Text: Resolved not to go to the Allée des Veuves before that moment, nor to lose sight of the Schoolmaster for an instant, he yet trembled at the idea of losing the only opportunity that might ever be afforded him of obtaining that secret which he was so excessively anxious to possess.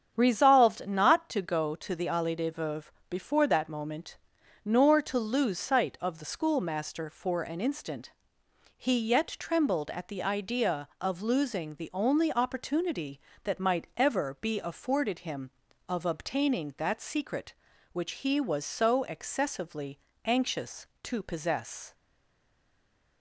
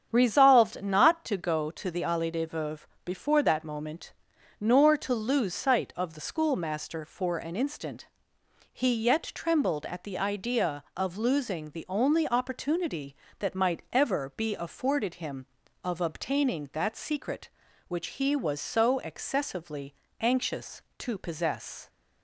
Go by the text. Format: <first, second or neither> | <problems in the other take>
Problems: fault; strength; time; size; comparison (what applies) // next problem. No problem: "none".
second | starts louder than the rest; strong; until 1.1 s; 8 dB; strong in the second // pauses between "Veuves" and "before"; slight; at 2.9 s; 0.18 s long; slight in the second // pauses between "excessively" and "anxious"; slight; at 19.9 s; 0.28 s long; slight in the second // stays silent after the last word; noticeable; from 21.9 s on; 1.3 s long